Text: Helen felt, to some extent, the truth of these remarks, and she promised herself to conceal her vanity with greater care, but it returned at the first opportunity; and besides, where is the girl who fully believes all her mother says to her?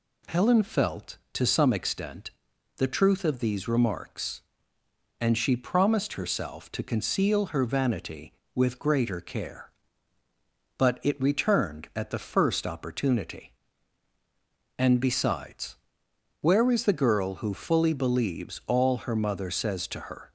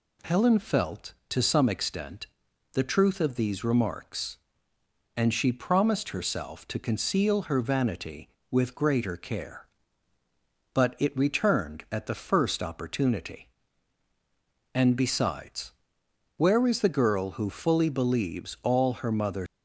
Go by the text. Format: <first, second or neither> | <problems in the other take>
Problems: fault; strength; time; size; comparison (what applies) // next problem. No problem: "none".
first | stops before "says to her"; at 19.4 s